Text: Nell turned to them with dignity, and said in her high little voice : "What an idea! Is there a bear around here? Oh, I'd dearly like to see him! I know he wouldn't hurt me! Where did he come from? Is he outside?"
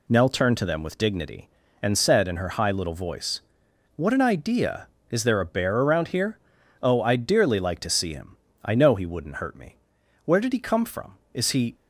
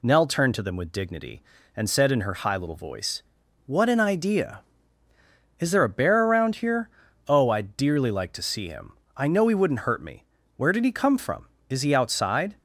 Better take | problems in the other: second | stops before "outside"; at 11.7 s

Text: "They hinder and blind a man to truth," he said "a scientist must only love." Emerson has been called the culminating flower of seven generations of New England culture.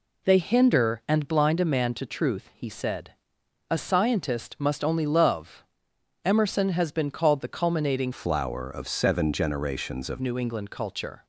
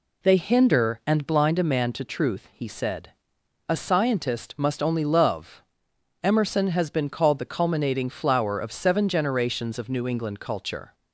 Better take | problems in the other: second | pauses between "said" and "a"; noticeable; at 3.1 s; 0.58 s long; noticeable in the second // changes voice from "flower" to "of"; from 8.1 to 10.2 s; 2.1 s long

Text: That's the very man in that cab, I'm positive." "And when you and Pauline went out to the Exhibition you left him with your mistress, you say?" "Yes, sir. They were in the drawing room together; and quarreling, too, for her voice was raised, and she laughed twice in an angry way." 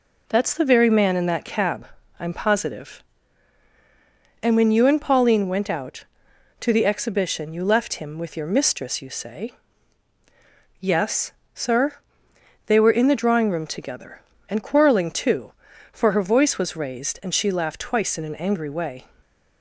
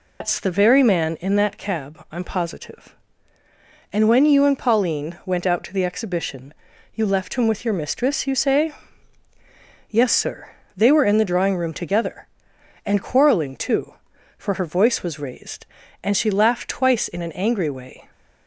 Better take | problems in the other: first | loses the start of "That's"; at 0.2 s; 145 ms // pauses between "Exhibition" and "you"; at 6.5 s; 0.42 s long

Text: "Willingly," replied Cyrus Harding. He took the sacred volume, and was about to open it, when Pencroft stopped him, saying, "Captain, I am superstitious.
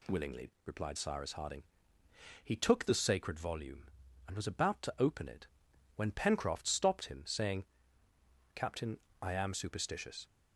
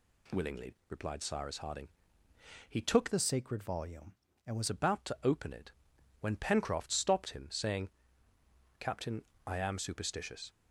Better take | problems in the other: first | changes voice from "the" to "was"; from 3.1 to 4.6 s; 1.5 s long

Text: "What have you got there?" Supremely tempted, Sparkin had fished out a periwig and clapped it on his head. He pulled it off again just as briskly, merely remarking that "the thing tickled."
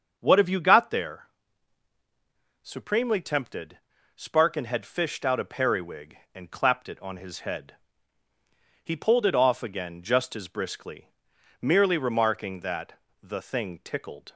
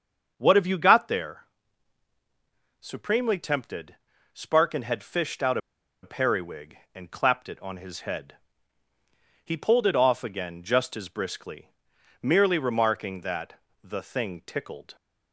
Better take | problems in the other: first | starts louder than the rest; until 1.3 s; 7 dB; also in the first // pauses between "out" and "a"; at 5.5 s; 0.44 s long // pauses between "that" and "the"; slight; at 13.5 s; 0.24 s long; slight in the first

